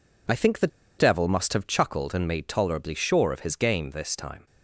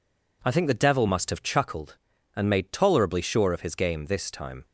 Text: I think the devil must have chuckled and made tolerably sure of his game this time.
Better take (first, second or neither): second